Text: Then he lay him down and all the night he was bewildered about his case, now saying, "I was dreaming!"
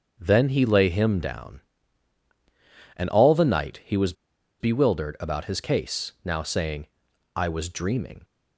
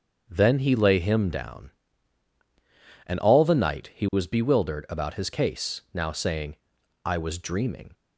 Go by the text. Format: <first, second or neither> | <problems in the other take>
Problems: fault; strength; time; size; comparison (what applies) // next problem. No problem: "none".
second | starts louder than the rest; until 1.2 s; 7 dB; also in the second // pauses between "was" and "bewildered"; noticeable; at 4.1 s; 0.47 s long